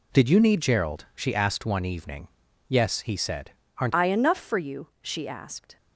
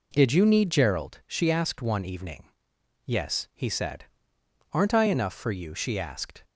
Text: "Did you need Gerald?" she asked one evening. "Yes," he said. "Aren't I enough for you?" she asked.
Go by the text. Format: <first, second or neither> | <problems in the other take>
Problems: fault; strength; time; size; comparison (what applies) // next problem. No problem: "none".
second | changes voice at "I"; from 3.9 s on; 1.8 s long